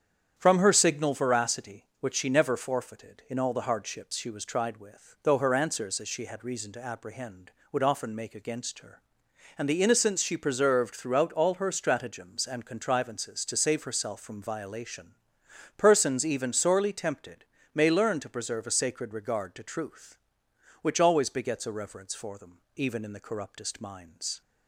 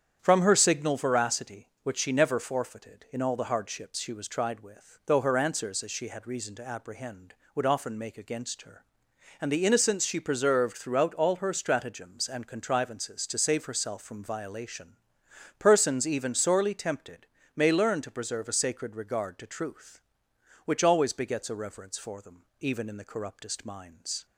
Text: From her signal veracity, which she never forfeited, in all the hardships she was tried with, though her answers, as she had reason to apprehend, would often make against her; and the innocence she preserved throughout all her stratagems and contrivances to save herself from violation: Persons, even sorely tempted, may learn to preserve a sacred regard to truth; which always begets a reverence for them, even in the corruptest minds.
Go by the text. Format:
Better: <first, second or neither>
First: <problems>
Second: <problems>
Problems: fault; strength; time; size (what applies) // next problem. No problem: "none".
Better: neither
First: starts louder than the rest; strong; until 1.3 s; 8.5 dB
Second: starts louder than the rest; strong; until 1.2 s; 8.5 dB